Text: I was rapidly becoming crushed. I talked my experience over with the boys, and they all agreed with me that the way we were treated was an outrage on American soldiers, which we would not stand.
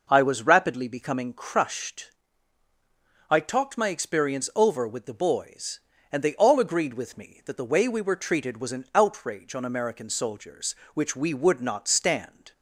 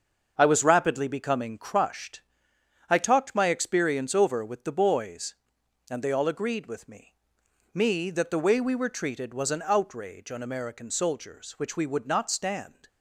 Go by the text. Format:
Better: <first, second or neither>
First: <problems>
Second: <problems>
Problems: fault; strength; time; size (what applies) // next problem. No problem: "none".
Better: first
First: none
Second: starts louder than the rest; until 1.3 s; 6.5 dB // says "me" twice; at 7.7 s